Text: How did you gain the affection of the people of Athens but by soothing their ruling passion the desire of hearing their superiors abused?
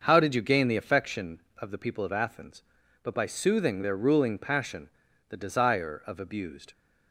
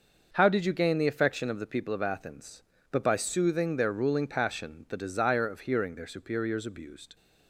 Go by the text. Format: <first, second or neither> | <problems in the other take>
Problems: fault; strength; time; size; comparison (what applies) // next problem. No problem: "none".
second | starts louder than the rest; until 1.0 s; 6.5 dB; noticeable in the second // pauses between "passion" and "the"; at 4.8 s; 0.40 s long // skips "hearing their superiors"; at 6.2 s